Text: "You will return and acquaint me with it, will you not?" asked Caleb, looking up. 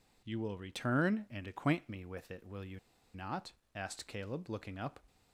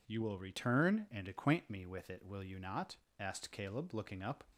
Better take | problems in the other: second | pauses between "you" and "not"; slight; at 2.7 s; 0.35 s long

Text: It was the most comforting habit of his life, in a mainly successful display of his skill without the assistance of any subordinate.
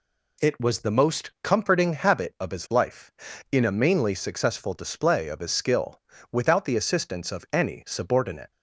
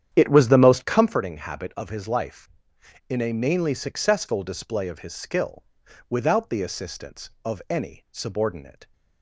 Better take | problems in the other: first | starts louder than the rest; strong; until 1.2 s; 9.5 dB // pauses between "skill" and "without"; at 5.6 s; 0.44 s long; slight in the first

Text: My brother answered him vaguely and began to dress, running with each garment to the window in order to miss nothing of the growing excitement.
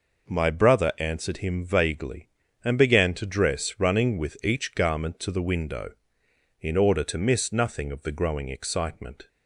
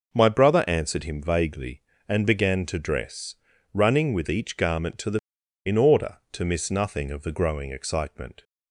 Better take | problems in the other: first | skips "window"; at 5.4 s

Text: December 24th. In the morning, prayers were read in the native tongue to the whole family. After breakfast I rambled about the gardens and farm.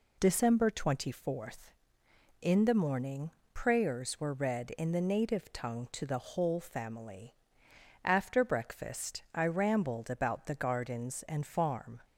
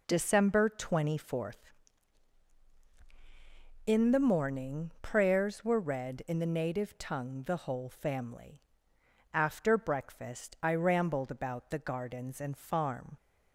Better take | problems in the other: first | skips "to"; at 7.4 s

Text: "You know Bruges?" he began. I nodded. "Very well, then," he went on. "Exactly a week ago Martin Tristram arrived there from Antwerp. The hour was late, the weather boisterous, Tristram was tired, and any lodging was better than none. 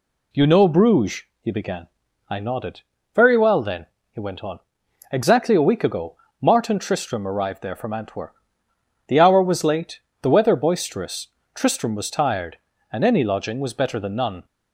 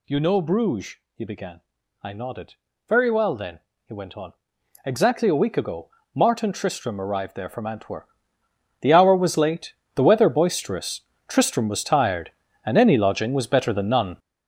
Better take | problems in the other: first | gets louder; strong; throughout; 9.5 dB // pauses between "ago" and "Martin"; slight; at 5.8 s; 0.26 s long; slight in the first

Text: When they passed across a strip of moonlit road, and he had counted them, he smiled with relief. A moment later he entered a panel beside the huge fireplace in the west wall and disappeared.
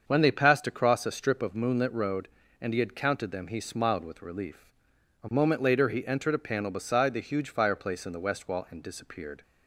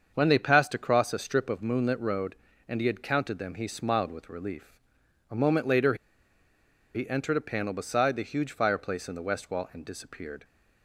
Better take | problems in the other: first | starts louder than the rest; until 1.1 s; 7 dB; also in the first // pauses between "later" and "he"; at 5.9 s; 0.99 s long

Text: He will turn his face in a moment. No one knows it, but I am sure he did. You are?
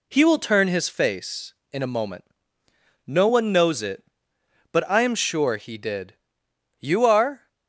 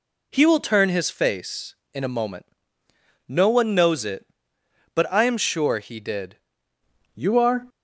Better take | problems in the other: first | changes voice at "You"; from 7.1 s on; 0.5 s long

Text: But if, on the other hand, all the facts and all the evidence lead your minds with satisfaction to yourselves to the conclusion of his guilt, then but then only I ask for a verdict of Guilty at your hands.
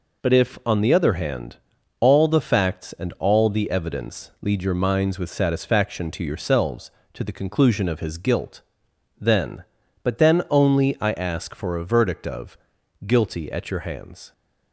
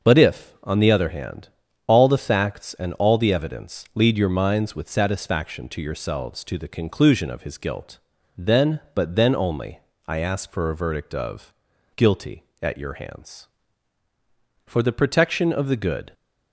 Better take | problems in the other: first | starts louder than the rest; until 1.1 s; 6.5 dB // pauses between "only" and "I"; slight; at 9.7 s; 0.28 s long // pauses between "of" and "Guilty"; at 11.5 s; 0.44 s long; noticeable in the first // goes on to say "For the protection of the good"; from 14.6 s on; 1.4 s long

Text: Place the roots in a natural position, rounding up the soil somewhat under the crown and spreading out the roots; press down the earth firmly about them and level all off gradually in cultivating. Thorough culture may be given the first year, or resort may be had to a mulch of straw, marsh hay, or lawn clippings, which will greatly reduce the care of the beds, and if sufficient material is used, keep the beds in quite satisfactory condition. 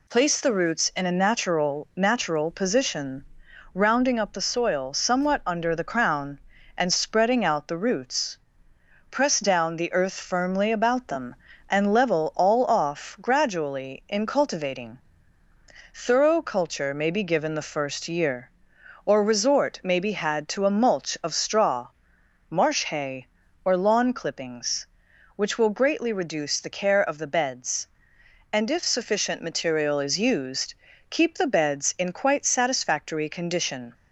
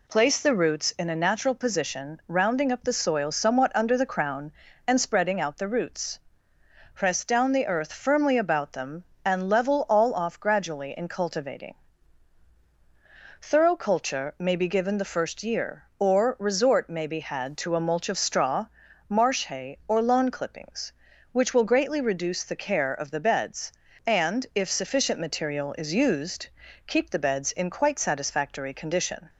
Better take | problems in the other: second | says "natural" twice; at 1.9 s

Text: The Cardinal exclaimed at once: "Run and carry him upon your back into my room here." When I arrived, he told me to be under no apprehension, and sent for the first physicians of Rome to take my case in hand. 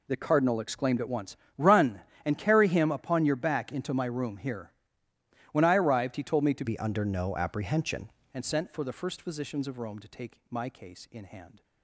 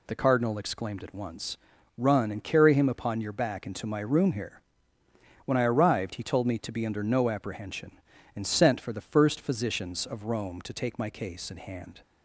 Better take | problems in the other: second | changes voice from "be" to "apprehension"; from 6.6 to 8.0 s; 1.4 s long

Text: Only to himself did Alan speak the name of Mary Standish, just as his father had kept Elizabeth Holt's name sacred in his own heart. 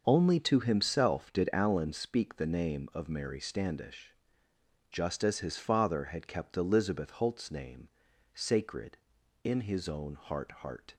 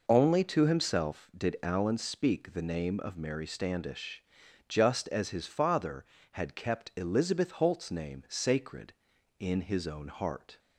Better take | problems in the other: second | starts louder than the rest; until 1.0 s; 6.5 dB // pauses between "name" and "sacred"; noticeable; at 7.8 s; 0.46 s long // says "heart" twice; at 10.5 s

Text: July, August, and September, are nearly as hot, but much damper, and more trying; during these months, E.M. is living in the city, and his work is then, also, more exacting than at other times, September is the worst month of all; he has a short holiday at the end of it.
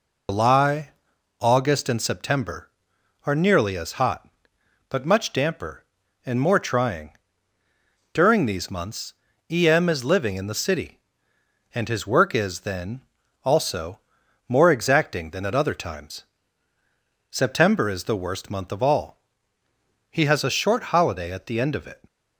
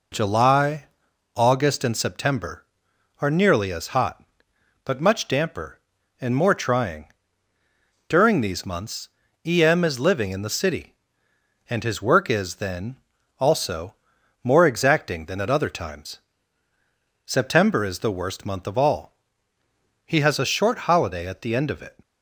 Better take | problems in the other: second | loses the start of "July"; at 0.2 s; 125 ms

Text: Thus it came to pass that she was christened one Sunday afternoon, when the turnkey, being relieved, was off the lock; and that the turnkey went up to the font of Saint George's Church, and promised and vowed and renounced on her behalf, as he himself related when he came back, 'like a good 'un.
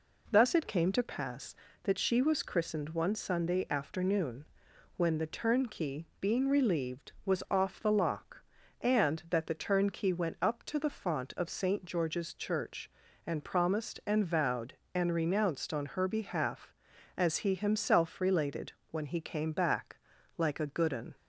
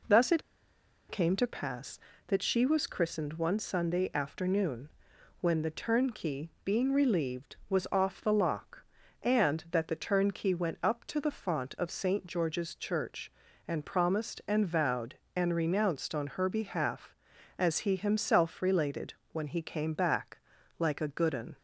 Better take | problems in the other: first | pauses between "it" and "came"; noticeable; at 0.4 s; 0.68 s long // pauses between "related" and "when"; slight; at 19.1 s; 0.18 s long; slight in the first

